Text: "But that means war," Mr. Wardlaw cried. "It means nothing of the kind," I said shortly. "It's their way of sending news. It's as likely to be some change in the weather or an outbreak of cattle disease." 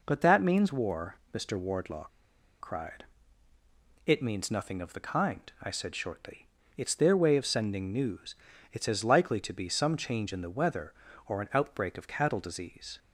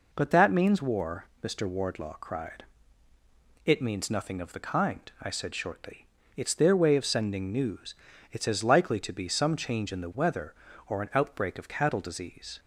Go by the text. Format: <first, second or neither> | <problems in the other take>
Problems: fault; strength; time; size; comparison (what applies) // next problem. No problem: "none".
second | pauses between "Wardlaw" and "cried"; noticeable; at 2.0 s; 0.51 s long